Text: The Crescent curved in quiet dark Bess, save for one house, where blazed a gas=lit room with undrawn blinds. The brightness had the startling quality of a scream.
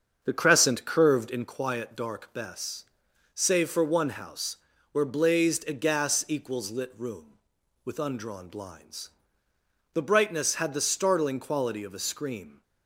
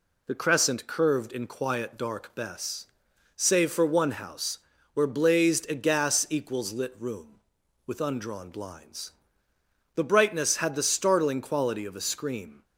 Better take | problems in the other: second | starts louder than the rest; until 1.6 s; 7 dB

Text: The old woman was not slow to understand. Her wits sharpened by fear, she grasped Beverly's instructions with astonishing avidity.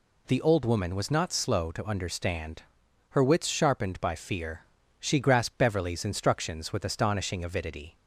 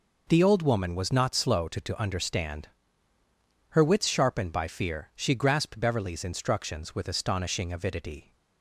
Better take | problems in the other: first | says "to" twice; at 1.8 s

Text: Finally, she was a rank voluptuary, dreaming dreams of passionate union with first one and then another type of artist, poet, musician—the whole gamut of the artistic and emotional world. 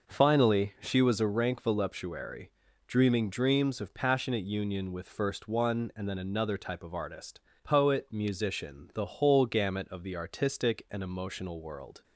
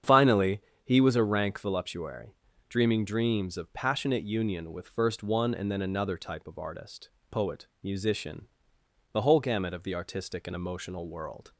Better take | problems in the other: first | starts louder than the rest; strong; until 1.2 s; 8 dB // says "he" for "she"; at 0.8 s

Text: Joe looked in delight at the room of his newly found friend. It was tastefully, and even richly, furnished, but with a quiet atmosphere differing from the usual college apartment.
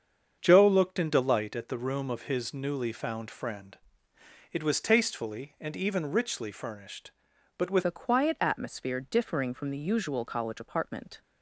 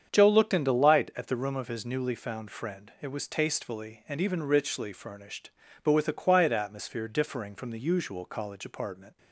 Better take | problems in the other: second | starts louder than the rest; strong; until 1.4 s; 7.5 dB; strong in the second // changes voice at "a"; from 7.8 s on; 3.4 s long

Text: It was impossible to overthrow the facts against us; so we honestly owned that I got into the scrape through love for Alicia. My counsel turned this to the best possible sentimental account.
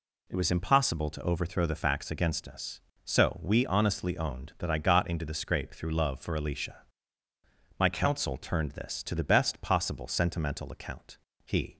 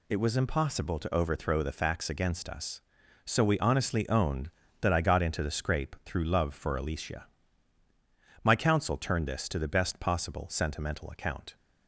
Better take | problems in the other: second | goes on to say "He"; slight; from 11.4 s on; 0.32 s long

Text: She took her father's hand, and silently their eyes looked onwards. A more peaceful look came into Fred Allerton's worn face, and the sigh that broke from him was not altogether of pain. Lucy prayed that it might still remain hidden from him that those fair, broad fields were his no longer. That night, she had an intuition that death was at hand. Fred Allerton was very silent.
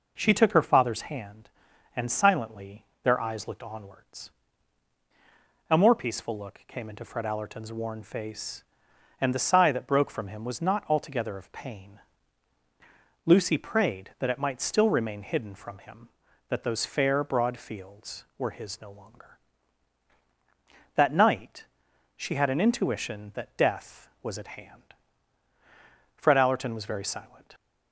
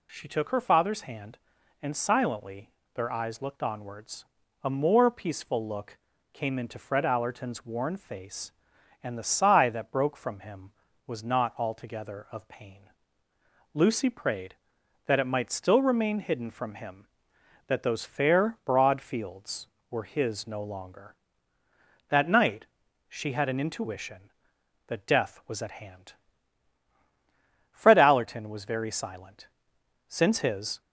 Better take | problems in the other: first | pauses between "silently" and "their"; slight; at 2.7 s; 0.24 s long; slight in the first // pauses between "look" and "came"; slight; at 5.9 s; 0.34 s long // goes on to say "Since his"; noticeable; from 30.0 s on; 0.72 s long

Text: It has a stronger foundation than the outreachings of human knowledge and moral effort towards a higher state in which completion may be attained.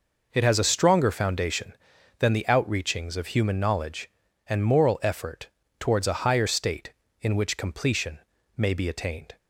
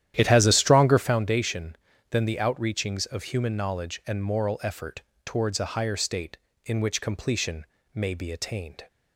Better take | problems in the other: first | starts louder than the rest; strong; until 1.2 s; 11 dB // pauses between "effort" and "towards"; slight; at 5.0 s; 0.24 s long; slight in the first // pauses between "completion" and "may"; slight; at 7.6 s; 0.30 s long; also in the first

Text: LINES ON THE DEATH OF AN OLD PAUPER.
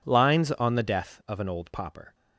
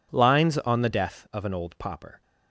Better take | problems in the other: neither | none

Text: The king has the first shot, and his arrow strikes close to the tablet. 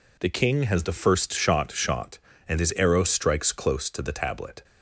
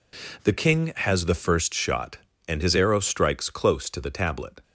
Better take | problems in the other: second | says "shot" twice; at 1.7 s

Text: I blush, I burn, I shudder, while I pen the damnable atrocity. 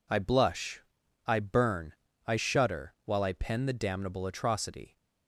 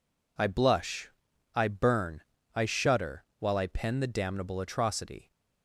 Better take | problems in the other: neither | none

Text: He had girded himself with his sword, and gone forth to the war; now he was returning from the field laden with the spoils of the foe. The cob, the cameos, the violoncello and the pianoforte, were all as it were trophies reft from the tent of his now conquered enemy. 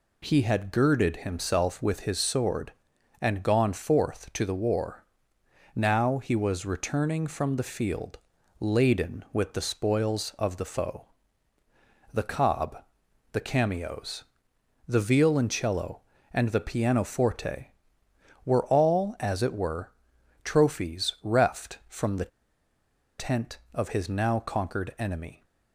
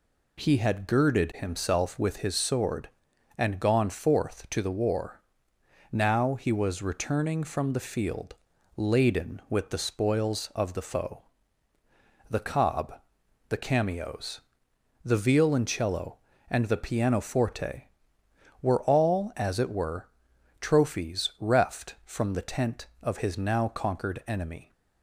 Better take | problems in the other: second | pauses between "field" and "laden"; at 8.1 s; 0.38 s long; also in the second // pauses between "were" and "trophies"; noticeable; at 19.9 s; 0.54 s long; noticeable in the second // pauses between "the" and "tent"; noticeable; at 22.3 s; 0.89 s long

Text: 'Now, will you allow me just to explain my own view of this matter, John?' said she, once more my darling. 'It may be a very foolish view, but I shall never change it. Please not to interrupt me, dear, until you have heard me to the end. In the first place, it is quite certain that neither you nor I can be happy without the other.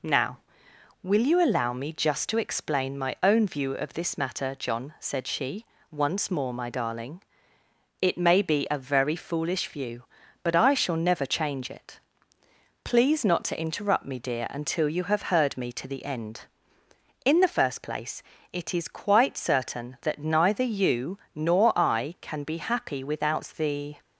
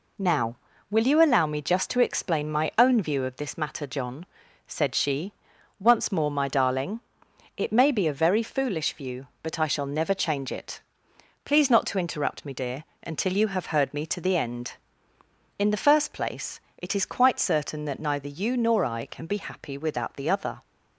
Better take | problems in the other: second | pauses between "you" and "nor"; slight; at 21.1 s; 0.16 s long // stops before "other"; at 24.0 s

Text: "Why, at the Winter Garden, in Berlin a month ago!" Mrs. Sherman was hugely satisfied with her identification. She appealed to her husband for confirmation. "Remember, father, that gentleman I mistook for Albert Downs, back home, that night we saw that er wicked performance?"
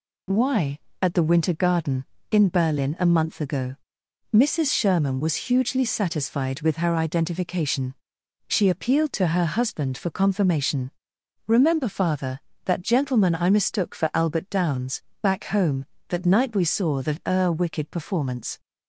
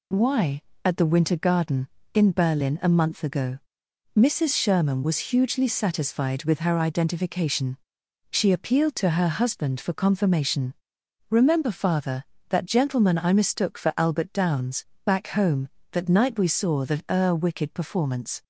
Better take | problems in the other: neither | none

